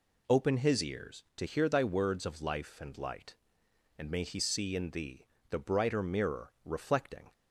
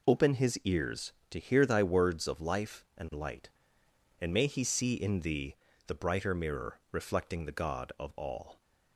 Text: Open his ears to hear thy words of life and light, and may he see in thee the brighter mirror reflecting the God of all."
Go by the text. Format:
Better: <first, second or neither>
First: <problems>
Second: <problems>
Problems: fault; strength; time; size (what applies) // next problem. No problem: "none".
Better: second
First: pauses between "thee" and "the"; slight; at 5.2 s; 0.24 s long // stops before "the God of all"; at 7.3 s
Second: pauses between "thee" and "the"; slight; at 5.5 s; 0.32 s long